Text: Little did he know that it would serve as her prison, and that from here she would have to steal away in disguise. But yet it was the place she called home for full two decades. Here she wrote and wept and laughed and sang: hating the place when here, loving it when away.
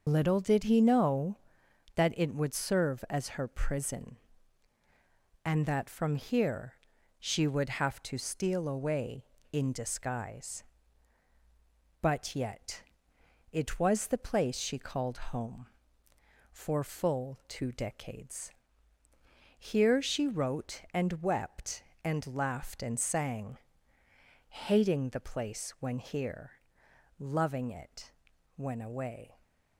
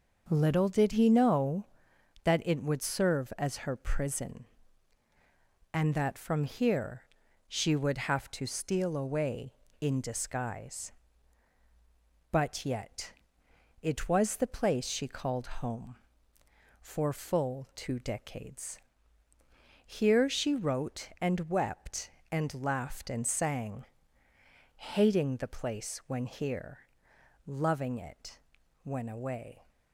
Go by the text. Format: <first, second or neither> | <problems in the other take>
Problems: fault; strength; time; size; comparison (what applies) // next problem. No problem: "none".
second | loses the start of "Little"; at 0.0 s; 90 ms // pauses between "here" and "she"; at 6.7 s; 0.44 s long; also in the second // pauses between "yet" and "it"; noticeable; at 12.8 s; 0.68 s long; noticeable in the second // pauses between "it" and "when"; noticeable; at 28.1 s; 0.46 s long; noticeable in the second